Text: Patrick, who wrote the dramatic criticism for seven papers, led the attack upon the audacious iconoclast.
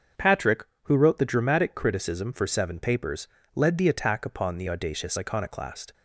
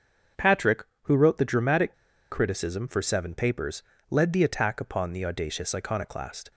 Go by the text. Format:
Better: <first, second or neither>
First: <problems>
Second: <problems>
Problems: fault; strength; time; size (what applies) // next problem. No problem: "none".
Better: first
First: starts louder than the rest; until 1.3 s; 6.5 dB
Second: starts louder than the rest; until 1.5 s; 6.5 dB // pauses between "dramatic" and "criticism"; slight; at 1.9 s; 0.35 s long